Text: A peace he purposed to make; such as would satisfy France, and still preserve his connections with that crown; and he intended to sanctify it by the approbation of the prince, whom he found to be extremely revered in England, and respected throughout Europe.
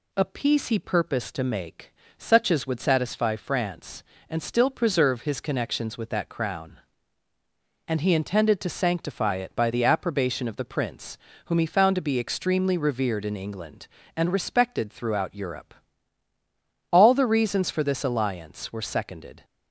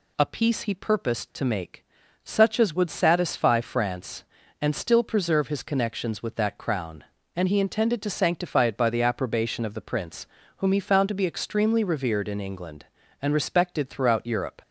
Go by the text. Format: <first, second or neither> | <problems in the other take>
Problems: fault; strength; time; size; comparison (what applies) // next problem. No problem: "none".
second | goes on to say "All the reasons for this alliance were seconded"; strong; from 16.9 s on; 2.5 s long